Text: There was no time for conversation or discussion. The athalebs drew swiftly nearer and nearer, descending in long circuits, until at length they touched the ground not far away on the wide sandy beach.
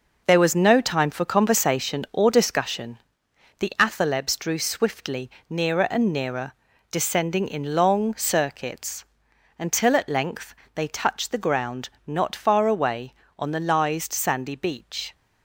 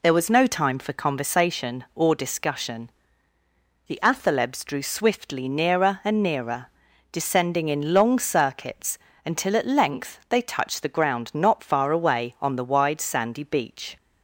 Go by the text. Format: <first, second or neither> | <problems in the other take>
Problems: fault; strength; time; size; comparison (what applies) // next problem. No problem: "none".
second | pauses between "swiftly" and "nearer"; slight; at 5.2 s; 0.20 s long // pauses between "length" and "they"; slight; at 10.5 s; 0.20 s long // pauses between "ground" and "not"; slight; at 11.8 s; 0.18 s long // says "lised" for "wide"; at 13.5 s